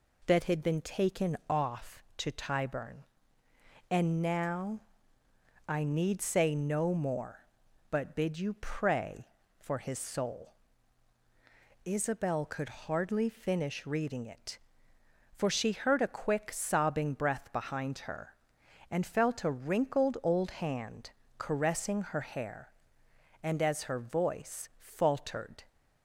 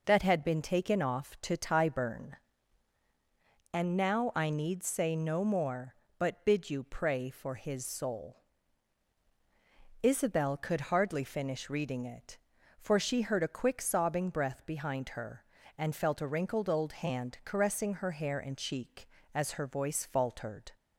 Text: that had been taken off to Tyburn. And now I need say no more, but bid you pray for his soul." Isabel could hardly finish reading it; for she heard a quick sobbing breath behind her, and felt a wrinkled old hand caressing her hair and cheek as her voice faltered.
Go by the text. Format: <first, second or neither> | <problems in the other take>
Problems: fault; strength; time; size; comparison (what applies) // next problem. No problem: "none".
second | pauses between "now" and "I"; noticeable; at 4.8 s; 0.86 s long // pauses between "hand" and "caressing"; slight; at 21.1 s; 0.26 s long // skips "cheek"; at 23.6 s